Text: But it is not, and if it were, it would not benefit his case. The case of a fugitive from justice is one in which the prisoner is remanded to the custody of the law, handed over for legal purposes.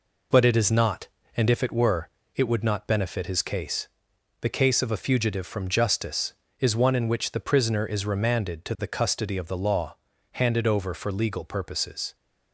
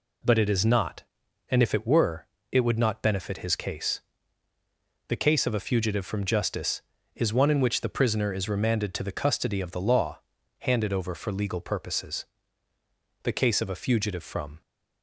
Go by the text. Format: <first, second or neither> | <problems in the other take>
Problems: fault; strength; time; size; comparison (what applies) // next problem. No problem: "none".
first | goes on to say "The case of a fugitive from"; from 13.2 s on; 1.3 s long